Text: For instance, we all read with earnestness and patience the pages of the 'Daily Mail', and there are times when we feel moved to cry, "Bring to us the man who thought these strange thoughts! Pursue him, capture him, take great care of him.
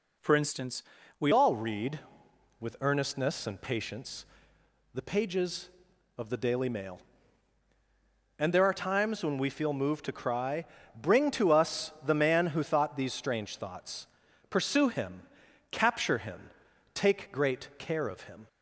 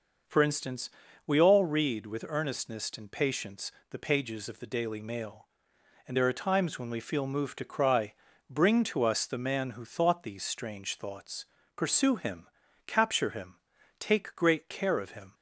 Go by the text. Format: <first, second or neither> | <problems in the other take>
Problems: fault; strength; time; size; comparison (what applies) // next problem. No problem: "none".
second | changes voice at "all"; from 1.3 s on; 17.1 s long // pauses between "patience" and "the"; noticeable; at 4.2 s; 0.68 s long; slight in the second